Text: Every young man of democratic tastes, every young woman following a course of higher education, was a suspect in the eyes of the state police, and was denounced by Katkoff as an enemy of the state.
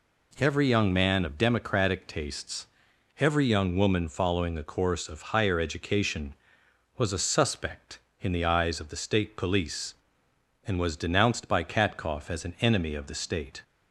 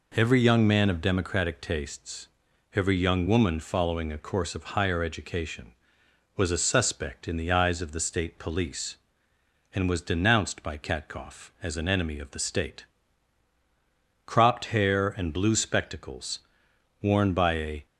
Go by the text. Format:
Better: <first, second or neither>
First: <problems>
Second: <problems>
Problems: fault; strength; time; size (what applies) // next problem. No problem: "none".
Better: first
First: none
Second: goes on to say "Cropped hair and blue spectacles worn by a"; strong; from 14.2 s on; 3.6 s long